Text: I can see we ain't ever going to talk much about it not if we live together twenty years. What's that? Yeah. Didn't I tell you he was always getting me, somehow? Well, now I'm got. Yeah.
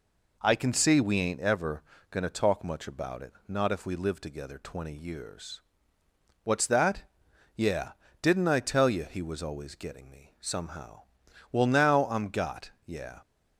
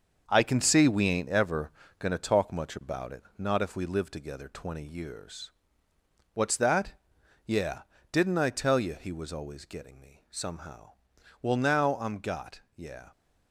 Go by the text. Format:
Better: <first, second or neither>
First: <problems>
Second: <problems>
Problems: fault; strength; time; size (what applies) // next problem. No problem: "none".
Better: first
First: pauses between "ever" and "going"; slight; at 1.8 s; 0.28 s long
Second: gets quieter; throughout; 7 dB // pauses between "ever" and "going"; slight; at 1.6 s; 0.28 s long